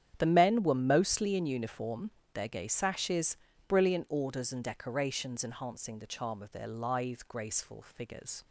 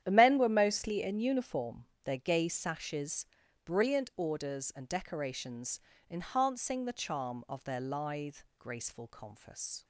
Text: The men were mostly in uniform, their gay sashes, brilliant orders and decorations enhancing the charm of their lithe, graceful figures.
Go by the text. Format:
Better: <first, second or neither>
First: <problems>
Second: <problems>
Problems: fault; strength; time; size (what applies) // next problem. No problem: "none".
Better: first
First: starts louder than the rest; strong; until 1.1 s; 9.5 dB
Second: starts louder than the rest; strong; until 1.0 s; 10.5 dB // pauses between "decorations" and "enhancing"; slight; at 5.7 s; 0.32 s long // says "confus" for "figures"; at 9.0 s